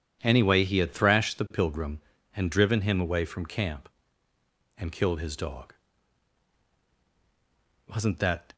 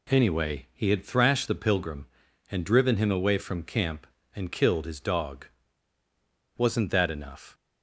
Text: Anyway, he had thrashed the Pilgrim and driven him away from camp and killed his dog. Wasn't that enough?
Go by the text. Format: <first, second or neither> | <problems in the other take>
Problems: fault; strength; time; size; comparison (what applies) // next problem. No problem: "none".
second | stops before "enough"; at 8.5 s